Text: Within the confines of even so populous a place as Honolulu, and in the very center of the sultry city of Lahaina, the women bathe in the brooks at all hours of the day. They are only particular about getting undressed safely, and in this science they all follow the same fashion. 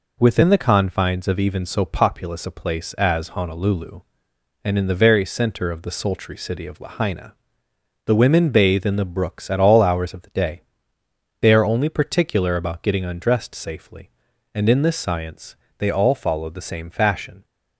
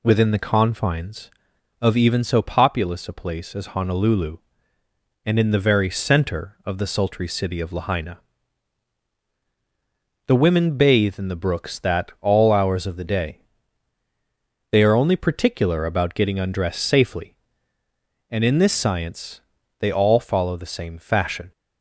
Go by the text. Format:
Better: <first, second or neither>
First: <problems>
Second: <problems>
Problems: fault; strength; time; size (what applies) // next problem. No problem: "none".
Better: first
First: pauses between "science" and "they"; slight; at 15.5 s; 0.24 s long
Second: says "that" for "at"; at 11.7 s // pauses between "science" and "they"; slight; at 19.4 s; 0.36 s long